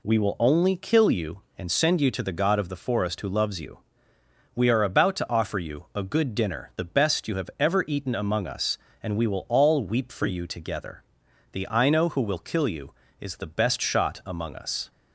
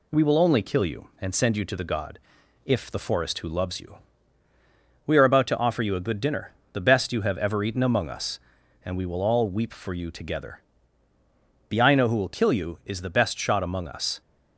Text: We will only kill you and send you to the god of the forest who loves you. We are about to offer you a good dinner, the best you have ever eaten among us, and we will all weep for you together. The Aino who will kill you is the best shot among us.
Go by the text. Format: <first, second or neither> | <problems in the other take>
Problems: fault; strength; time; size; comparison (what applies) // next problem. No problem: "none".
first | says "if" for "of"; at 2.6 s